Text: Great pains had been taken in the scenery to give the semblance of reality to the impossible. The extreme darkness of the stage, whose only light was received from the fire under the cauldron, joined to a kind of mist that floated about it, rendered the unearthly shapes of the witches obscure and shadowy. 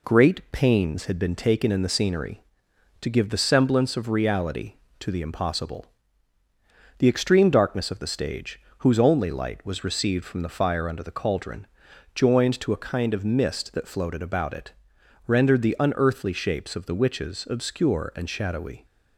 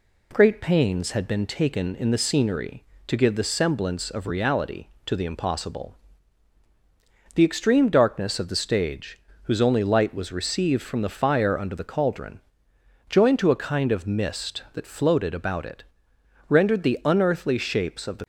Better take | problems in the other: first | stops before "witches obscure and shadowy"; at 18.2 s

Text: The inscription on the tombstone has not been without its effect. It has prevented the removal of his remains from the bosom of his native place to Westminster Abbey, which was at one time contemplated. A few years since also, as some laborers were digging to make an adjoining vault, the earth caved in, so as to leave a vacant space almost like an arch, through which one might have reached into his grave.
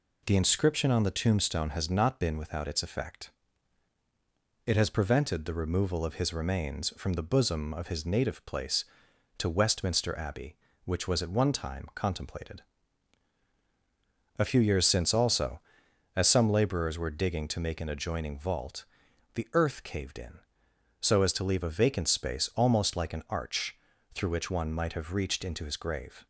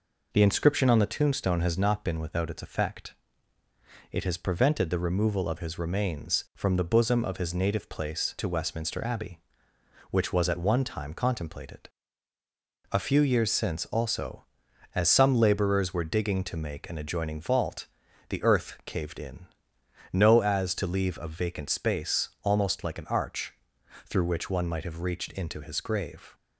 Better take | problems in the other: first | says "no" for "so"; at 20.1 s

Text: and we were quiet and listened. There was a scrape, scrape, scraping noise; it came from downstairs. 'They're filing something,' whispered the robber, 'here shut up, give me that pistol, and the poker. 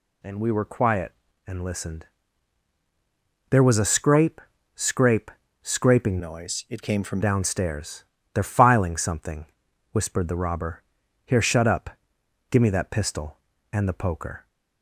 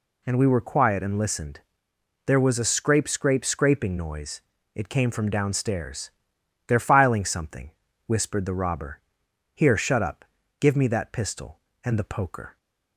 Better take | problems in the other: second | changes voice from "noise" to "from"; from 6.1 to 7.2 s; 1.1 s long

